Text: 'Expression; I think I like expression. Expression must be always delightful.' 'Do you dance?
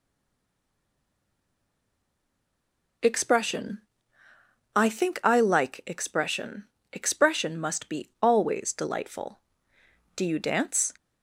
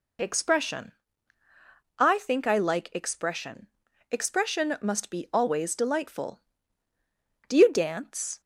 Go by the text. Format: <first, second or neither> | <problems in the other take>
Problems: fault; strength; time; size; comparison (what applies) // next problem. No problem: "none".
second | stays silent before the first word; strong; until 3.0 s; 3.0 s long